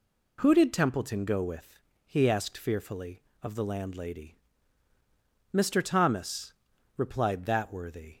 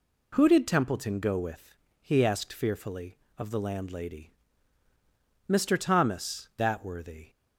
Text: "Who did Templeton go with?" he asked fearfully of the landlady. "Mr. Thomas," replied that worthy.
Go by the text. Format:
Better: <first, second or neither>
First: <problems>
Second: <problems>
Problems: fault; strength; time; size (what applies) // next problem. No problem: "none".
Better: first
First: none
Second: skips "replied"; at 6.5 s